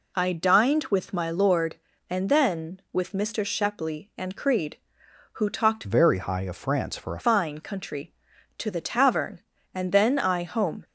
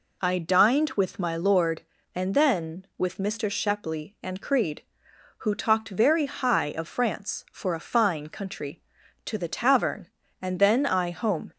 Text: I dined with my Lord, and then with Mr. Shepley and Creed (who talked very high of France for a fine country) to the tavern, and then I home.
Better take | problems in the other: second | changes voice from "very" to "a"; from 5.8 to 7.2 s; 1.4 s long

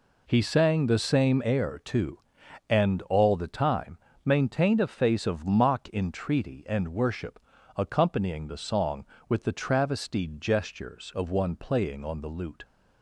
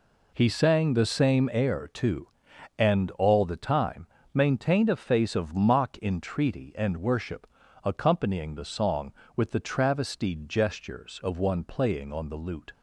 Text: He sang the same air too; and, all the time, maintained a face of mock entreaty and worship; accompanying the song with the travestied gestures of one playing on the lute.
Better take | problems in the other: neither | none

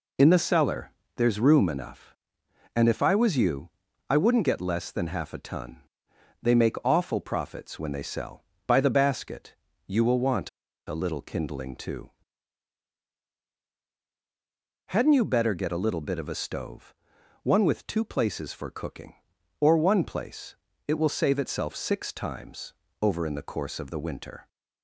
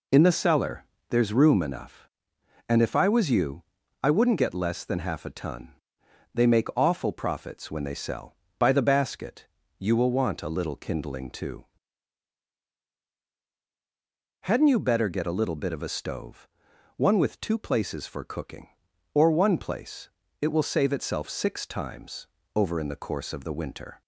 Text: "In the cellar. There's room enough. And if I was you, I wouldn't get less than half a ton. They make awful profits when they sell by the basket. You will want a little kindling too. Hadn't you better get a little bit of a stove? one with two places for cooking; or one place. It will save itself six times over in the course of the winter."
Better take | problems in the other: second | pauses between "want" and "a"; at 10.4 s; 0.38 s long // pauses between "times" and "over"; slight; at 22.7 s; 0.28 s long; slight in the second

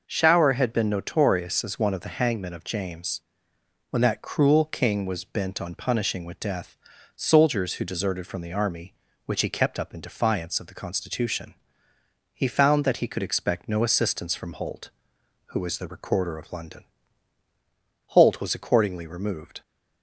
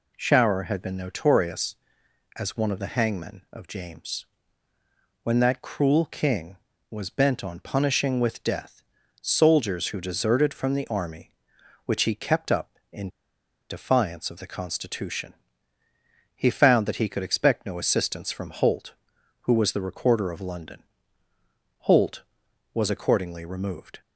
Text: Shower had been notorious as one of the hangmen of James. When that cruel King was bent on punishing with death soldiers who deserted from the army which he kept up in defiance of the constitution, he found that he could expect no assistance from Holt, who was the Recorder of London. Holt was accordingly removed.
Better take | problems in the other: first | pauses between "death" and "soldiers"; at 8.8 s; 0.44 s long; also in the first // pauses between "in" and "defiance"; noticeable; at 13.0 s; 0.60 s long

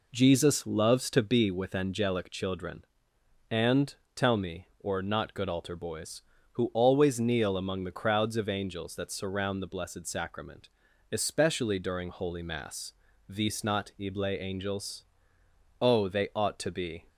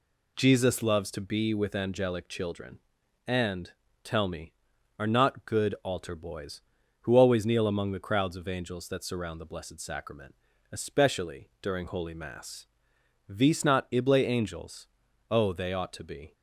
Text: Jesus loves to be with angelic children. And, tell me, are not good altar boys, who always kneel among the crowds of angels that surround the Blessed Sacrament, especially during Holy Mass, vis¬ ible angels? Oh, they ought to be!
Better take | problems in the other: second | says "or" for "are"; at 4.7 s

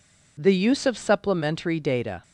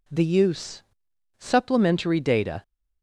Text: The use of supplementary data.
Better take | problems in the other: first | skips "of"; at 1.1 s

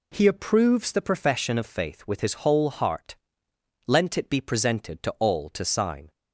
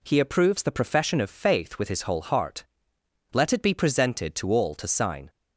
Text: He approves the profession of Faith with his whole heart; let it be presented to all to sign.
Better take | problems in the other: second | says "lent" for "let"; at 3.8 s

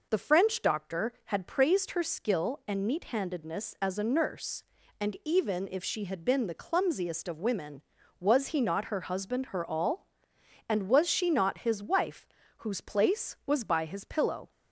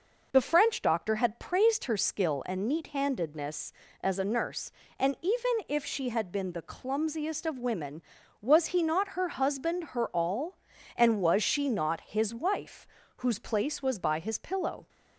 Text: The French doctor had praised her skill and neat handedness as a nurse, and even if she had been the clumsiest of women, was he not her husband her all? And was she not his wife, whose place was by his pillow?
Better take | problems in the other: neither | none

